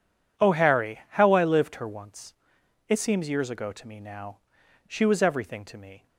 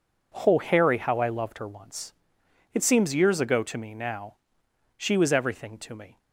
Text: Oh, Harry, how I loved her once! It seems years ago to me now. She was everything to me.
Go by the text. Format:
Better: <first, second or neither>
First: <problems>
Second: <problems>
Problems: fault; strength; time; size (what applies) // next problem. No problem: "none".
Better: second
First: says "lived" for "loved"; at 1.4 s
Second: none